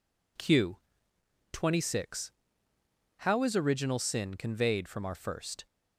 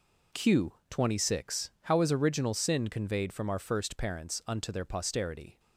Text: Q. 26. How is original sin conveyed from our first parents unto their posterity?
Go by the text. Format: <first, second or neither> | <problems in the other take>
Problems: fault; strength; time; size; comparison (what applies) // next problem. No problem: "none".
second | stops before "parents unto their posterity"; at 5.6 s